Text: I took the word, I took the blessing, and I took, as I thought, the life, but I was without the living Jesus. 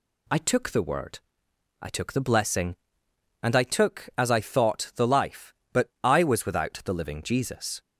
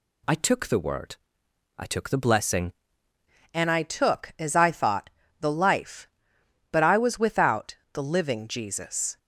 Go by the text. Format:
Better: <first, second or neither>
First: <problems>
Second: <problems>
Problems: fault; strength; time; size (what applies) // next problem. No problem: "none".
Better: first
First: none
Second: changes voice at "and"; from 3.5 s on; 5.6 s long // pauses between "without" and "the"; slight; at 7.7 s; 0.18 s long